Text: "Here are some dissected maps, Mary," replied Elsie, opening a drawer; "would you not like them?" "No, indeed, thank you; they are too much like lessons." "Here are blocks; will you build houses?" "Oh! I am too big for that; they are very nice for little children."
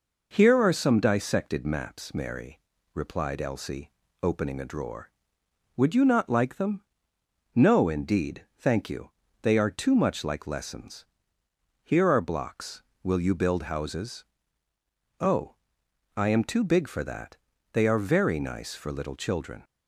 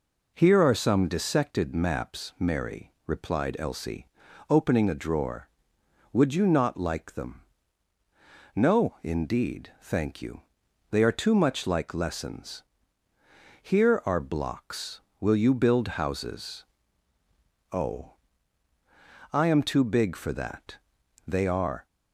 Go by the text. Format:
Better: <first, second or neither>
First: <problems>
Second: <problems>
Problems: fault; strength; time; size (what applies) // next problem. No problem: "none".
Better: first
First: none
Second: stops before "very nice for little children"; at 21.8 s